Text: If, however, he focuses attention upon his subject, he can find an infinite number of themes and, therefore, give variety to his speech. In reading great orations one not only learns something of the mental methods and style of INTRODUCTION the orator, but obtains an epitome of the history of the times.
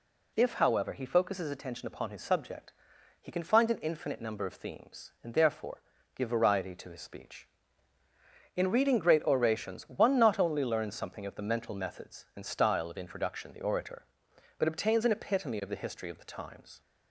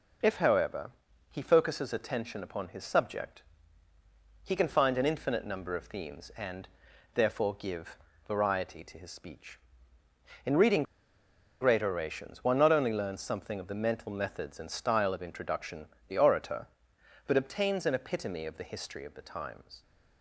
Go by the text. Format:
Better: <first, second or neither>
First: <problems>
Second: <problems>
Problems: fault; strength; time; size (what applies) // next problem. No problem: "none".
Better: first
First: none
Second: pauses between "give" and "variety"; slight; at 7.9 s; 0.30 s long // pauses between "reading" and "great"; noticeable; at 10.8 s; 0.78 s long // pauses between "INTRODUCTION" and "the"; slight; at 15.8 s; 0.22 s long